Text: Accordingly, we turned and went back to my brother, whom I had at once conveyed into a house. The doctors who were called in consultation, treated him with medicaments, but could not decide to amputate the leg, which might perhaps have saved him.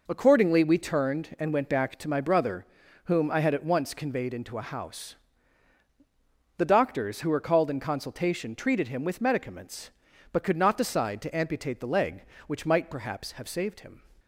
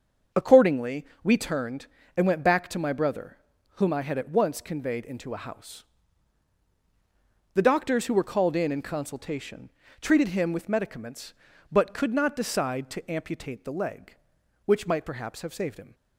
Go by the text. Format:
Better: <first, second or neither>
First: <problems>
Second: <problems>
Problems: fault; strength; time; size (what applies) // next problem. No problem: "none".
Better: first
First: none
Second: starts louder than the rest; until 1.5 s; 7 dB // says "in" twice; at 8.7 s